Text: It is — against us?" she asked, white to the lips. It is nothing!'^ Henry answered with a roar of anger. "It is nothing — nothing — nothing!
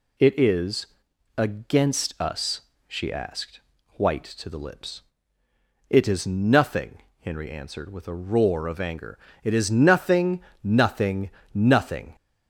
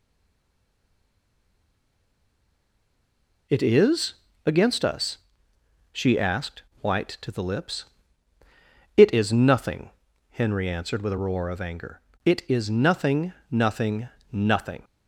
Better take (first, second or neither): first